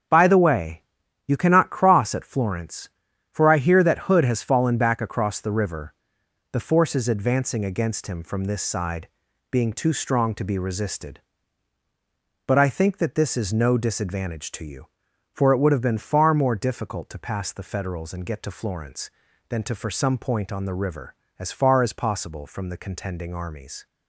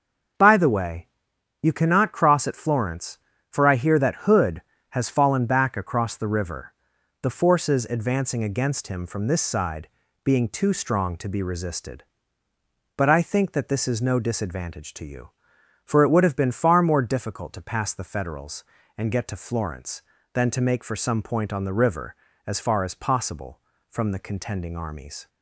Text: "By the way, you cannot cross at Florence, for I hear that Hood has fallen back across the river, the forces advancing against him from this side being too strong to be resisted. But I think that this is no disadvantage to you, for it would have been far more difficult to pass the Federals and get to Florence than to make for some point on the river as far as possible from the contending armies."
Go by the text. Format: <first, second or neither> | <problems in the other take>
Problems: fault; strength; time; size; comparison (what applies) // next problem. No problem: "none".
second | starts louder than the rest; strong; until 1.5 s; 7.5 dB; also in the second // pauses between "side" and "being"; at 9.0 s; 0.42 s long; also in the second // skips "make"; at 19.7 s